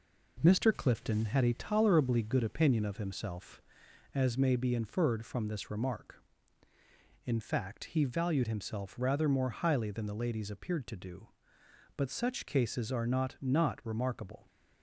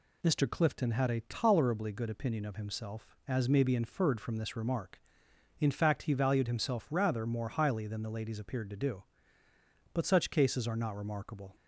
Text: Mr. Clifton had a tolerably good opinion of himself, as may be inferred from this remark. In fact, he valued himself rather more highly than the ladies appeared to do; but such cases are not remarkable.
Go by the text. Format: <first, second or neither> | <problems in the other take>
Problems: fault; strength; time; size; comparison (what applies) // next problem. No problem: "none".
second | says "not" twice; at 13.4 s